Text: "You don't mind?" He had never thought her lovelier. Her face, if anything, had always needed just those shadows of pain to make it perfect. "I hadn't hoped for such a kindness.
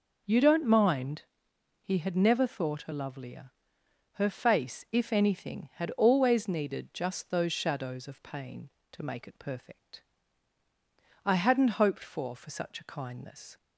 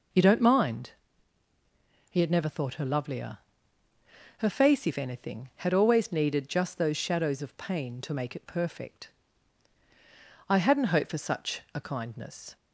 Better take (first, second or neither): second